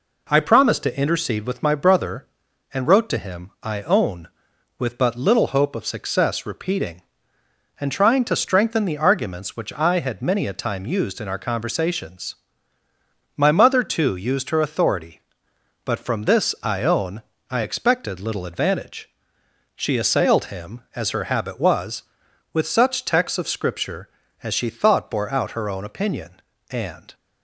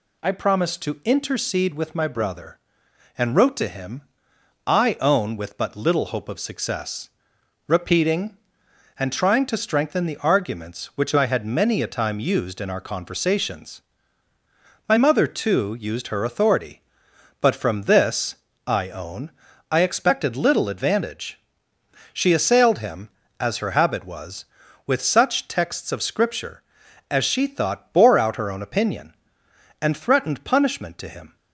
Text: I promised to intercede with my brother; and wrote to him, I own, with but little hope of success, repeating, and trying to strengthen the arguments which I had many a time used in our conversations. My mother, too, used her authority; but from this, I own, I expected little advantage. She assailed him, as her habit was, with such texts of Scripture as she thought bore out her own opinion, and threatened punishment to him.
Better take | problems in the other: second | stops before "threatened punishment to him"; at 27.1 s

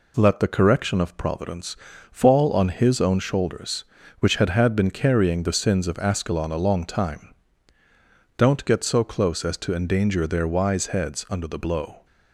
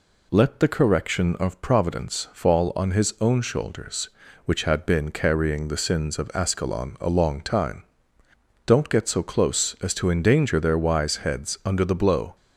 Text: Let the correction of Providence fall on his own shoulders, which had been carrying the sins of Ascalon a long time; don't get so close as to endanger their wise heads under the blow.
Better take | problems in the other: second | pauses between "Providence" and "fall"; slight; at 1.7 s; 0.34 s long // says "had" twice; at 4.4 s

